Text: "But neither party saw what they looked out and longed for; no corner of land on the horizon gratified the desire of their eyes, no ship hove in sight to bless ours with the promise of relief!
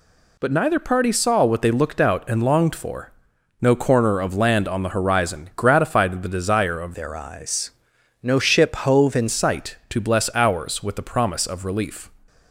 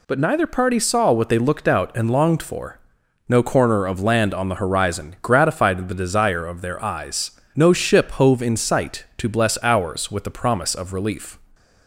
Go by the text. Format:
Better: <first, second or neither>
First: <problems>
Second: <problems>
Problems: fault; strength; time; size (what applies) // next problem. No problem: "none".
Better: second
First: changes voice from "their" to "in"; from 6.9 to 9.2 s; 2.3 s long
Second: none